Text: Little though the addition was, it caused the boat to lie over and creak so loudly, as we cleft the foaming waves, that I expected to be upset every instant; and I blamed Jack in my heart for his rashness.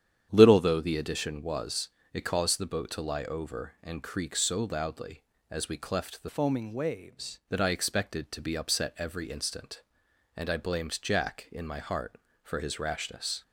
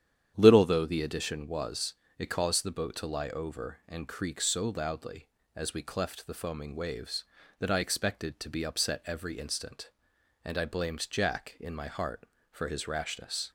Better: second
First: starts louder than the rest; strong; until 1.3 s; 9 dB // changes voice from "foaming" to "waves"; from 6.2 to 7.3 s; 1.1 s long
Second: starts louder than the rest; strong; until 1.3 s; 9.5 dB

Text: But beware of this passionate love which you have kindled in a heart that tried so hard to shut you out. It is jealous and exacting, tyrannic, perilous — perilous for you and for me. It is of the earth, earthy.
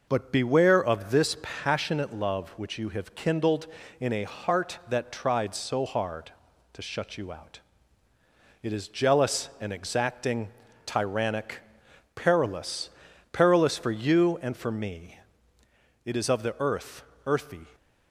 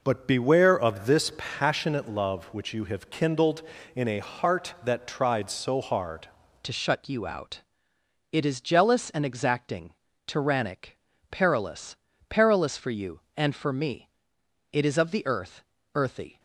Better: first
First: none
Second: changes voice at "to"; from 6.6 s on; 9.7 s long

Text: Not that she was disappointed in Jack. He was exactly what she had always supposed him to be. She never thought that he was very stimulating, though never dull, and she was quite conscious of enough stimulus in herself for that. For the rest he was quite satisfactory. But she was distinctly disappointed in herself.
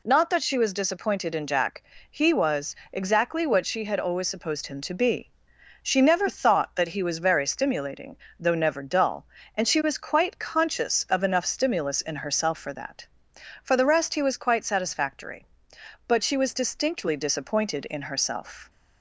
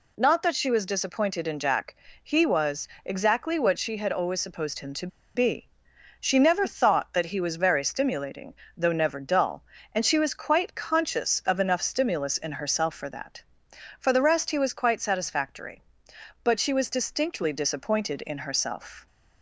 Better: first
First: pauses between "was" and "exactly"; slight; at 2.7 s; 0.16 s long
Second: pauses between "was" and "exactly"; slight; at 2.8 s; 0.16 s long // pauses between "to" and "be"; slight; at 5.0 s; 0.28 s long

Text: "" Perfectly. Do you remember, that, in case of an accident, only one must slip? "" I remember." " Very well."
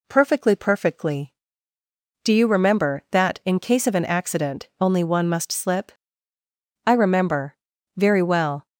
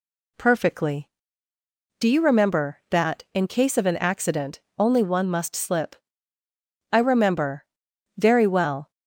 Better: second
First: says "Perfectly" twice; at 0.5 s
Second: none

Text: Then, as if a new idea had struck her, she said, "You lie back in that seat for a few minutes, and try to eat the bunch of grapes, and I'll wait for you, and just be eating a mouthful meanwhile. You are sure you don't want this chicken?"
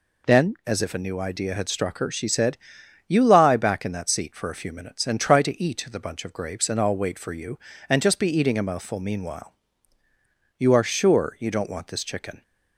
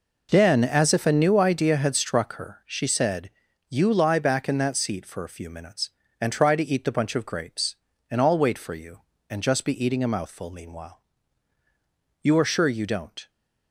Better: first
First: none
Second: stops before "want this chicken"; at 13.2 s

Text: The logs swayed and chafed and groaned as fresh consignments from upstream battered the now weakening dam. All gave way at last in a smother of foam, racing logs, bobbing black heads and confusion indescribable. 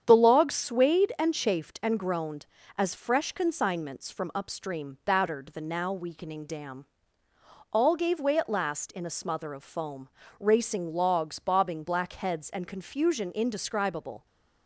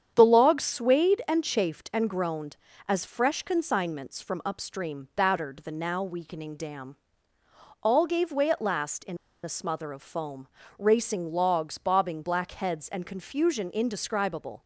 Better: first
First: starts louder than the rest; strong; until 1.0 s; 8.5 dB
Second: starts louder than the rest; strong; until 1.1 s; 8.5 dB // pauses between "in" and "a"; slight; at 9.1 s; 0.26 s long

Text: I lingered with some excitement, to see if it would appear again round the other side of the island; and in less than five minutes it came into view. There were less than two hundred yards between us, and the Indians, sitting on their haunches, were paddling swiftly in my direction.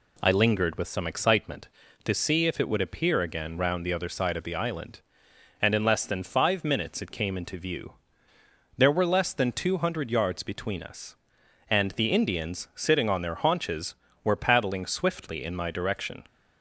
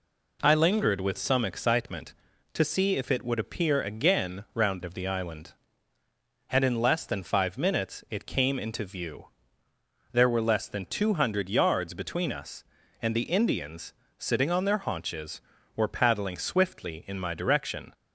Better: first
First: none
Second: skips "the other side"; at 4.8 s

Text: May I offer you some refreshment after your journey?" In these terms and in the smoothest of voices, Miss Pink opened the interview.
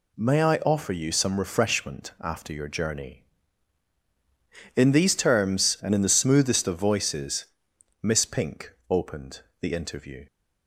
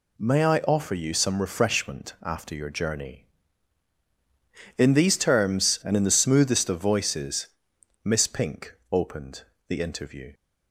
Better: neither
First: pauses between "opened" and "the"; slight; at 9.4 s; 0.20 s long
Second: pauses between "opened" and "the"; slight; at 9.4 s; 0.25 s long

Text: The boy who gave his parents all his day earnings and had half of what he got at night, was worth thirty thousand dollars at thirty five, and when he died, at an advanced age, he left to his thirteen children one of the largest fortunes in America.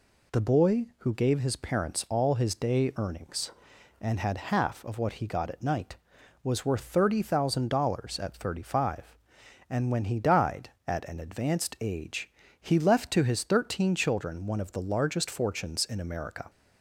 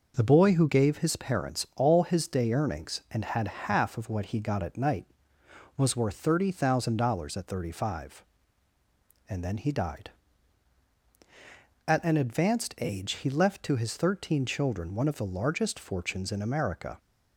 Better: first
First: none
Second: says "then" for "when"; at 9.4 s

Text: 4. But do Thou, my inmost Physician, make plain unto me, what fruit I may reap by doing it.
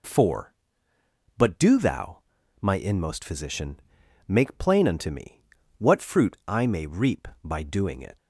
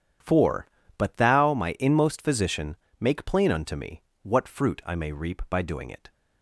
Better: first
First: none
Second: skips "do"; at 1.1 s

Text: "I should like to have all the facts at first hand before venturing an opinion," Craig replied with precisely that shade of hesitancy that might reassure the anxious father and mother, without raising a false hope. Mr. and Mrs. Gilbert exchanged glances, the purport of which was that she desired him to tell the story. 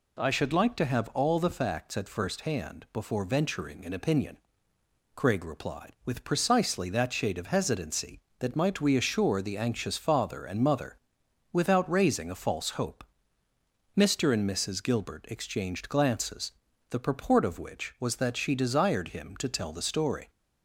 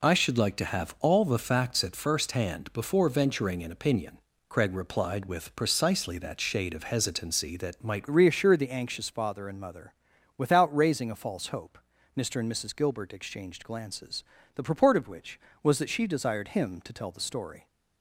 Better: first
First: none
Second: changes voice at "reassure"; from 8.1 s on; 9.5 s long

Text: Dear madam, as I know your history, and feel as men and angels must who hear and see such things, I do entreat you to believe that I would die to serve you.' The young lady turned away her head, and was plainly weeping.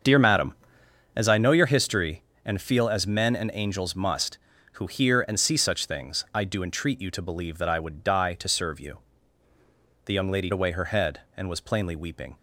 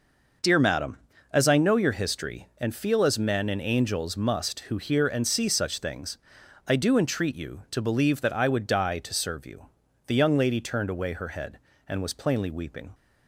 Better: second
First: starts louder than the rest; until 1.6 s; 7 dB // skips "turned"; at 10.5 s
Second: none

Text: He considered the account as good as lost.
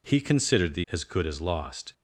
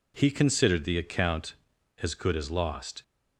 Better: second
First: skips "account"; at 0.8 s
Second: none

